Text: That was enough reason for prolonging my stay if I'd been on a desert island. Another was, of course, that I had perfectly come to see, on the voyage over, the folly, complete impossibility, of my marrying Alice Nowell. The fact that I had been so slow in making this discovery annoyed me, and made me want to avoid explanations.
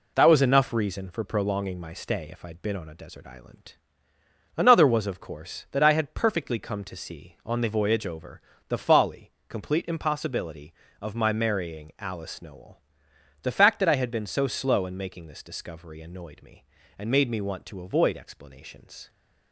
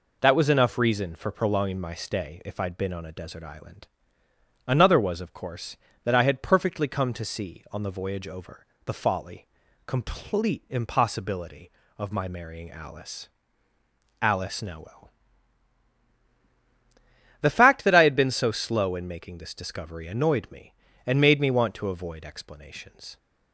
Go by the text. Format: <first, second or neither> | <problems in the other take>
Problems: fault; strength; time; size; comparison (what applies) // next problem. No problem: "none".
first | says "Alice" twice; at 14.2 s